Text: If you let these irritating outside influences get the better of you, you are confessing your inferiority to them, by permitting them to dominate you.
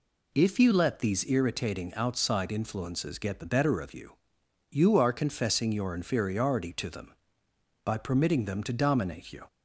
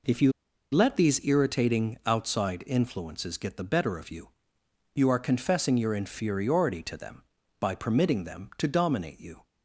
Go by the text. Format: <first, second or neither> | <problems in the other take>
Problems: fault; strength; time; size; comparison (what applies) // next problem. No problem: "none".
first | pauses between "you" and "let"; at 0.3 s; 0.41 s long